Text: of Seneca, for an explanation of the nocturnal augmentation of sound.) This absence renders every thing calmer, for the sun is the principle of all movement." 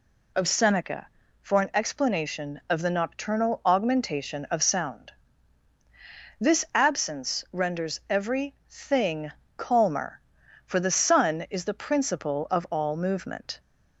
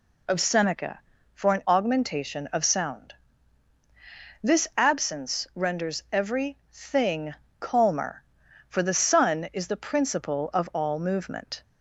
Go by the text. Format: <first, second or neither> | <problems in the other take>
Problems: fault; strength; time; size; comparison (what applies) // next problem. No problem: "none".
first | skips "explanation of the nocturnal"; at 1.6 s // pauses between "every" and "thing"; slight; at 6.5 s; 0.16 s long; slight in the first // pauses between "thing" and "calmer"; slight; at 7.3 s; 0.28 s long; slight in the first